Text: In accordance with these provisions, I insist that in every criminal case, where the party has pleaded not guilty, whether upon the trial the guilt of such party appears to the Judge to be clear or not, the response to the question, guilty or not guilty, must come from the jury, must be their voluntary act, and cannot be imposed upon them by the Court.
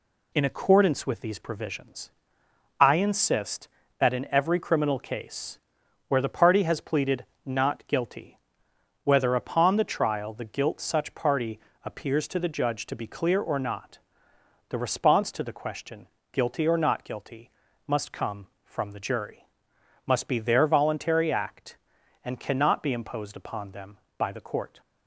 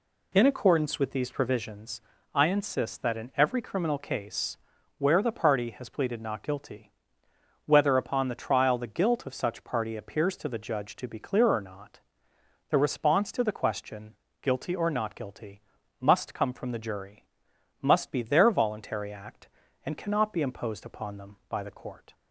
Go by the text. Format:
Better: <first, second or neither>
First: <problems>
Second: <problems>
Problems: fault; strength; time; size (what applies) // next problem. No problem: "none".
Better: second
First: pauses between "pleaded" and "not"; slight; at 7.2 s; 0.20 s long // skips "of"; at 10.8 s // pauses between "party" and "appears"; slight; at 11.5 s; 0.24 s long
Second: none